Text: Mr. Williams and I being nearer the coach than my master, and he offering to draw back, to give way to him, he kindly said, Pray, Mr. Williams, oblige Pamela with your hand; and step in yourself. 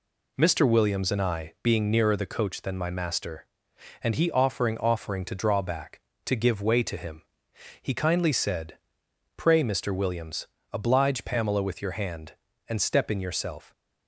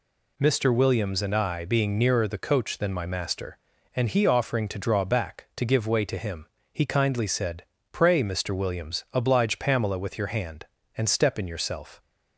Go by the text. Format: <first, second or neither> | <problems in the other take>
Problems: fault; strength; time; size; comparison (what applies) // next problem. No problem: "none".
second | says "offering" twice; at 4.7 s